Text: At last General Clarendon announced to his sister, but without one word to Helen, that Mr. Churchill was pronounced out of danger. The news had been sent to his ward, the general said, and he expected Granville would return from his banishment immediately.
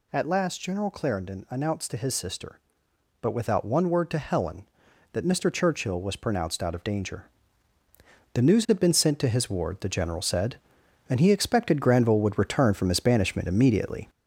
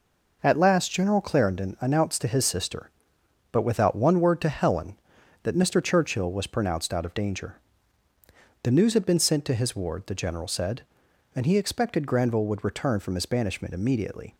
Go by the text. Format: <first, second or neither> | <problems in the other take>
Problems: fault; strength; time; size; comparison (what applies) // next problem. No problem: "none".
second | gets louder; noticeable; throughout; 4 dB